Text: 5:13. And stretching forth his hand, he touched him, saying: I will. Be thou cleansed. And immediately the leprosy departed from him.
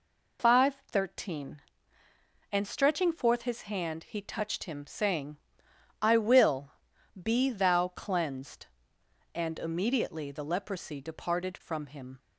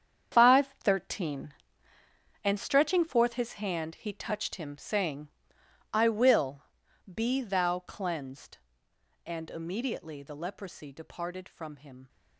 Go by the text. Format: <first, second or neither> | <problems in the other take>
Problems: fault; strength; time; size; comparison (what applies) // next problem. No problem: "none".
first | gets quieter; strong; throughout; 12 dB